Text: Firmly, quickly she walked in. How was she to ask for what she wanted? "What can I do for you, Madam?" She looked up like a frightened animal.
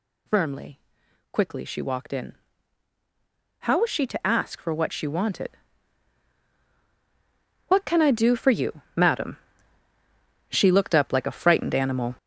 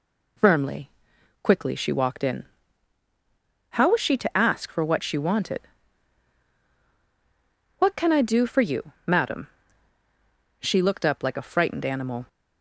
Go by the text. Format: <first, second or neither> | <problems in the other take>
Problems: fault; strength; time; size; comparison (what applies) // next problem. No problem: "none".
second | gets louder; strong; throughout; 7.5 dB